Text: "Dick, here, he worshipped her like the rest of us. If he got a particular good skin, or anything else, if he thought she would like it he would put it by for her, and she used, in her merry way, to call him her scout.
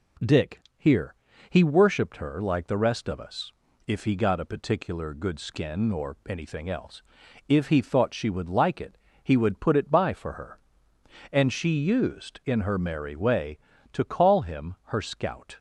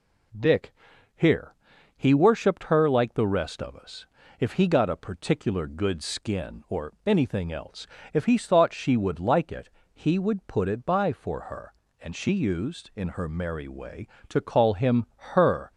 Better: first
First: pauses between "it" and "he"; slight; at 8.9 s; 0.24 s long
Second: pauses between "it" and "he"; slight; at 9.6 s; 0.22 s long // pauses between "him" and "her"; slight; at 15.0 s; 0.30 s long // stops before "scout"; at 15.7 s

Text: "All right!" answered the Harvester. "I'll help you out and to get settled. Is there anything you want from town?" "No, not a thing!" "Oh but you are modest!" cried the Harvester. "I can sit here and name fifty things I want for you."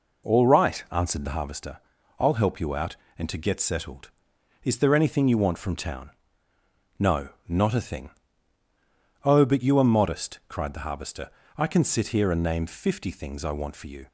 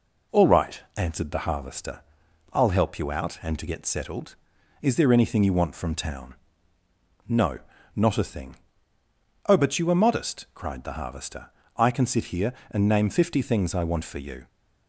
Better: neither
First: none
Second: none

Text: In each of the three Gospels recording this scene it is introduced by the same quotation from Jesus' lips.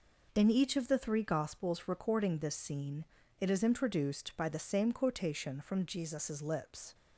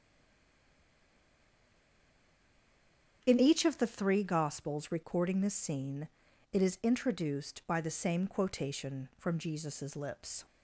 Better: first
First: pauses between "scene" and "it"; slight; at 3.0 s; 0.36 s long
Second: stays silent before the first word; strong; until 3.2 s; 3.2 s long // starts louder than the rest; strong; until 4.2 s; 8 dB // pauses between "scene" and "it"; at 6.0 s; 0.44 s long

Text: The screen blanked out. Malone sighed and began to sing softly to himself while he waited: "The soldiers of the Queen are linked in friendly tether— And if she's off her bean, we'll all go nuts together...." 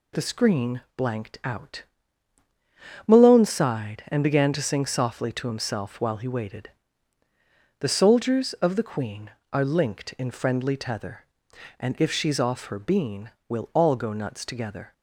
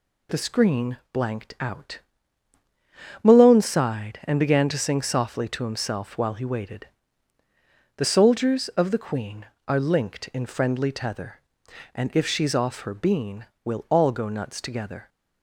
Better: neither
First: none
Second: none

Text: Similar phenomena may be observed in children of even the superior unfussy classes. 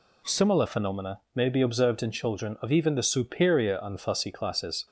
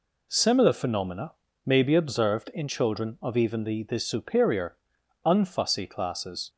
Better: first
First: none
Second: pauses between "phenomena" and "may"; slight; at 1.3 s; 0.32 s long // says "the" twice; at 3.8 s // pauses between "superior" and "unfussy"; noticeable; at 4.7 s; 0.48 s long

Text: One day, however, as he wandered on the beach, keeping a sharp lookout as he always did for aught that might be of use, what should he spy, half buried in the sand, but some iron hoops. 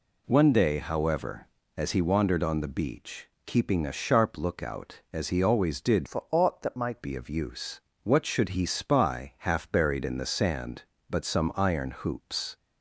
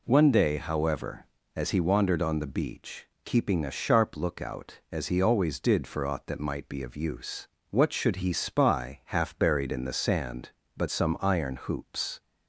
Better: second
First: changes voice from "for" to "might"; from 6.0 to 7.0 s; 1.0 s long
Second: none

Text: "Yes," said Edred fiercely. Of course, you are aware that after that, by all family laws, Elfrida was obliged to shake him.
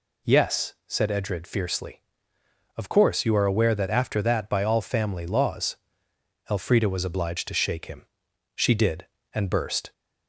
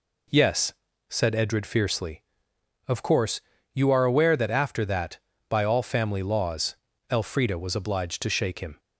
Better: second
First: goes on to say "She did and burst"; from 8.5 s on; 1.3 s long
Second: none

